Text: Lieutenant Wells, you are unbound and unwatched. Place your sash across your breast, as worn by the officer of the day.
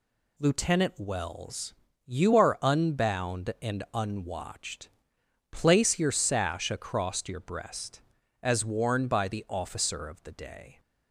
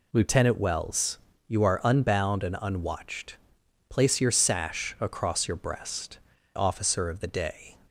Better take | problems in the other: first | skips "as worn by the"; at 6.3 s

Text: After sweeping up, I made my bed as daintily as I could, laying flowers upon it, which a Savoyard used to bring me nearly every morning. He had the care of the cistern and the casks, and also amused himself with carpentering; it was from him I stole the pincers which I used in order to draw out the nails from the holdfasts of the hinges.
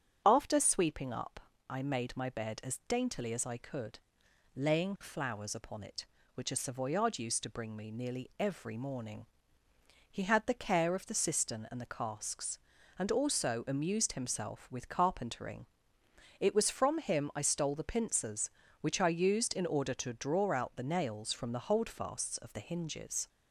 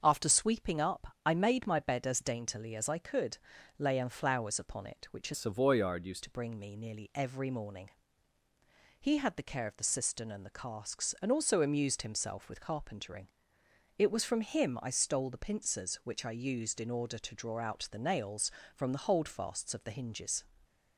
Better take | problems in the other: first | starts louder than the rest; until 1.0 s; 7 dB; strong in the first // changes voice from "Savoyard" to "used"; from 5.3 to 6.2 s; 0.9 s long

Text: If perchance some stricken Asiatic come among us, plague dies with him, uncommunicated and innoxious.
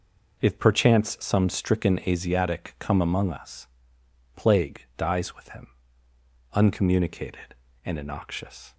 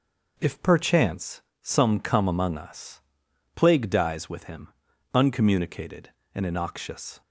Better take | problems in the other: first | pauses between "perchance" and "some"; slight; at 1.4 s; 0.22 s long // skips "stricken Asiatic"; at 1.9 s

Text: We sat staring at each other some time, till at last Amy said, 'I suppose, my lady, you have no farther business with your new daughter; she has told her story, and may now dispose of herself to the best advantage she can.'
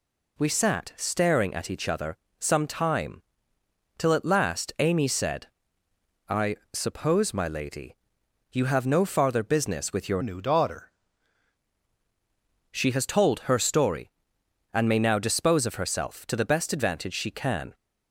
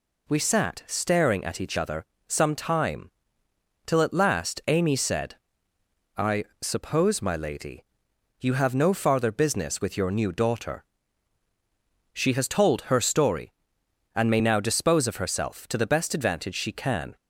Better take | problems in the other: second | pauses between "other" and "some"; slight; at 2.1 s; 0.22 s long; slight in the second // pauses between "I" and "suppose"; slight; at 6.5 s; 0.18 s long; slight in the second // changes voice from "new" to "daughter"; from 10.2 to 10.9 s; 0.7 s long

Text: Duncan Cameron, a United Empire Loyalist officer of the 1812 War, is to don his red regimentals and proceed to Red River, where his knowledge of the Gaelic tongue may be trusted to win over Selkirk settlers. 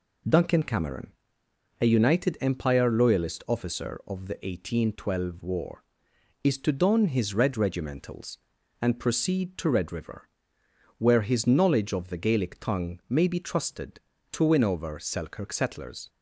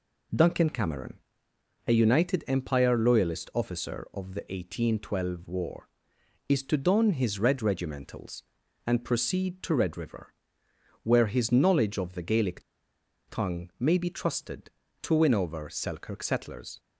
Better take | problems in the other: first | pauses between "Gaelic" and "tongue"; noticeable; at 12.6 s; 0.66 s long

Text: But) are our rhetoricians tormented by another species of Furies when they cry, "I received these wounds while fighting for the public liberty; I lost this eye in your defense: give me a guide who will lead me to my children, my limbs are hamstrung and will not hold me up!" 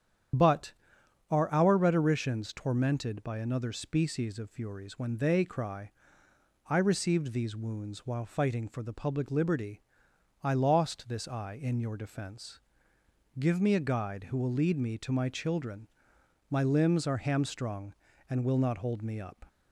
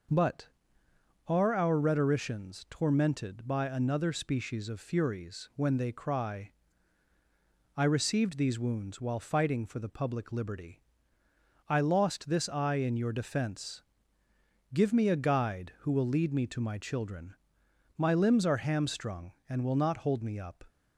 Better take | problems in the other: second | loses the start of "But"; at 0.3 s; 40 ms // starts louder than the rest; strong; until 1.9 s; 9 dB

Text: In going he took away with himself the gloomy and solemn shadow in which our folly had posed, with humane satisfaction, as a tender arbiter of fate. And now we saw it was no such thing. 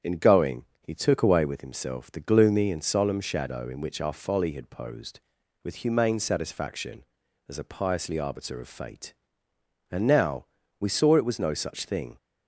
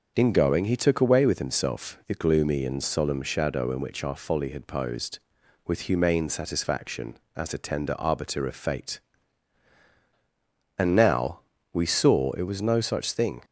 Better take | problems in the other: second | starts louder than the rest; strong; until 1.1 s; 8 dB; also in the second // pauses between "going" and "he"; slight; at 0.6 s; 0.16 s long // says "piously" for "tender"; at 7.6 s // pauses between "now" and "we"; slight; at 10.4 s; 0.36 s long; slight in the second

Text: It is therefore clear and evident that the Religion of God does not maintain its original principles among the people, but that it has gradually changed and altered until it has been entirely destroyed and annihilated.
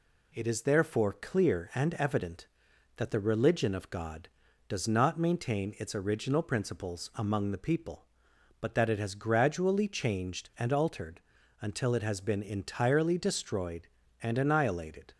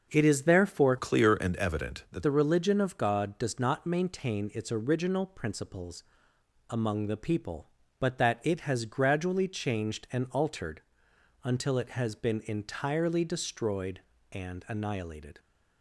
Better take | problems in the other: first | starts louder than the rest; until 1.1 s; 6.5 dB // changes voice from "clear" to "that"; from 0.9 to 2.2 s; 1.3 s long // pauses between "principles" and "among"; noticeable; at 6.0 s; 0.66 s long // pauses between "altered" and "until"; noticeable; at 10.8 s; 0.62 s long; also in the first

